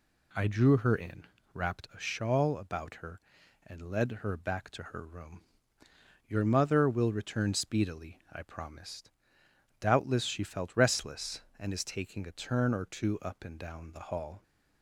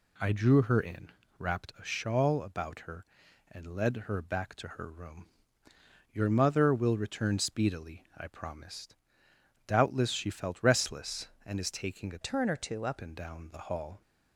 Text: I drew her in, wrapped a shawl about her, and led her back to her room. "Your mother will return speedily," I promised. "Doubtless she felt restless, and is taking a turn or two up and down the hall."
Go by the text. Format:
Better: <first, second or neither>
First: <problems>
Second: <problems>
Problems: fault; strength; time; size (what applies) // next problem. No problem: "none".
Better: first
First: none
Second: changes voice from "turn" to "up"; from 12.2 to 12.9 s; 0.7 s long